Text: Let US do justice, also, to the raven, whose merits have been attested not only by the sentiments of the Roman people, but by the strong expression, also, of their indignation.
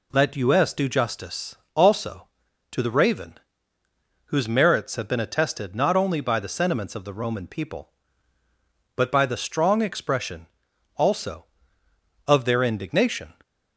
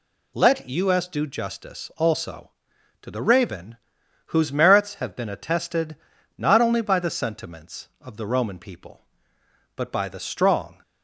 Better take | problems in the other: first | pauses between "attested" and "not"; at 5.9 s; 0.42 s long // stops before "expression also of their indignation"; at 10.8 s

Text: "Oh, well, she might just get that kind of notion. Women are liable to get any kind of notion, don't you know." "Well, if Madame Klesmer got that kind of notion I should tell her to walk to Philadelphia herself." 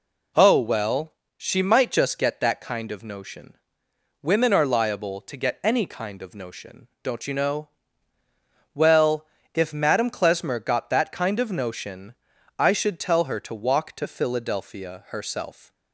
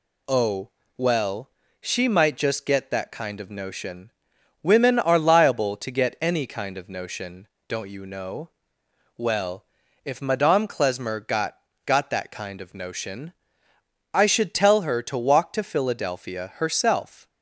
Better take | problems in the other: first | says "got" twice; at 11.8 s // pauses between "notion" and "I"; noticeable; at 13.3 s; 0.80 s long; noticeable in the first

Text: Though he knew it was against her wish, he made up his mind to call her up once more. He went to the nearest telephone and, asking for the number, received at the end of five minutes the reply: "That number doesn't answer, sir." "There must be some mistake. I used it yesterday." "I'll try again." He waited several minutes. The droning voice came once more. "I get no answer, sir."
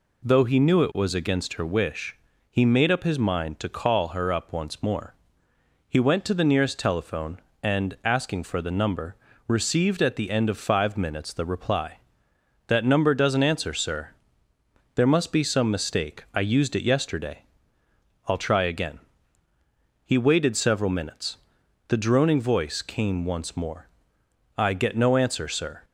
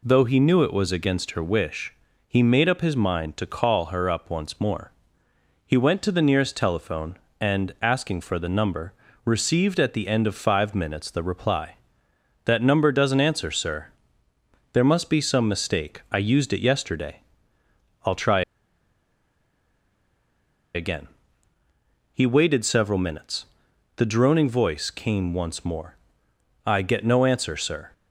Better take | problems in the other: first | pauses between "try" and "again"; strong; at 18.4 s; 2.3 s long

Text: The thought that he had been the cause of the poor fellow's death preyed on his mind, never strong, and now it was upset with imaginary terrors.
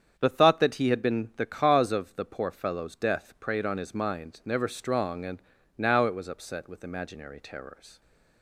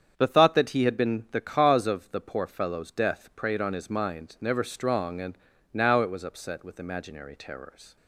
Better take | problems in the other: neither | starts louder than the rest; strong; the same in both // pauses between "and" and "now"; slight; the same in both

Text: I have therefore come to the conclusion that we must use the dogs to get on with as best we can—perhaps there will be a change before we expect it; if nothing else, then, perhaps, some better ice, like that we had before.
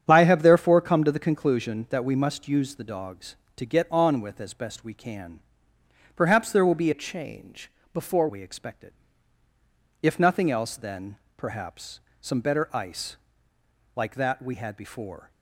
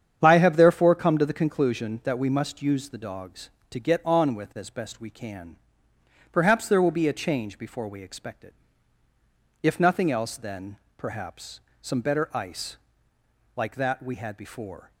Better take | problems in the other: second | starts louder than the rest; strong; until 1.0 s; 8.5 dB; strong in the second // changes voice from "a" to "before"; from 6.9 to 8.2 s; 1.3 s long // pauses between "change" and "before"; slight; at 7.7 s; 0.24 s long

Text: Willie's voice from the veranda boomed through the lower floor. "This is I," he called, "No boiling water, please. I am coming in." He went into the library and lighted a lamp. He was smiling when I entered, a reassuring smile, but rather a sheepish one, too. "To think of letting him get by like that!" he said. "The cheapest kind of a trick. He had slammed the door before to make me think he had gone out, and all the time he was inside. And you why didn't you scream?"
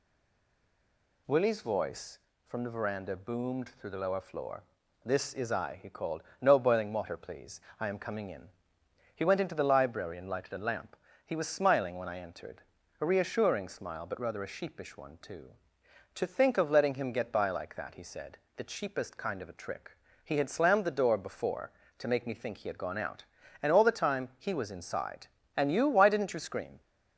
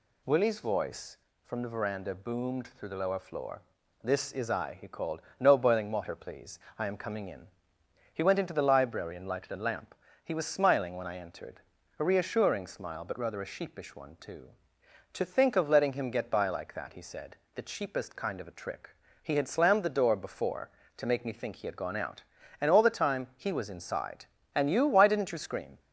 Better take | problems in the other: second | stays silent before the first word; noticeable; until 1.2 s; 1.2 s long

